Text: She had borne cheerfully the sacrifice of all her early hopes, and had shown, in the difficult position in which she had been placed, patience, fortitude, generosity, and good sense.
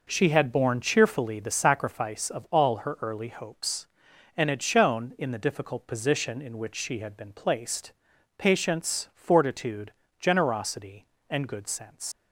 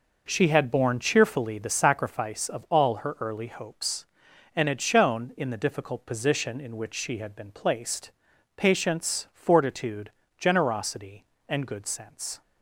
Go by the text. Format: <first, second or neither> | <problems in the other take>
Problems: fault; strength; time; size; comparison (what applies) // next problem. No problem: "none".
second | leaves "sense" unfinished; at 12.1 s; 105 ms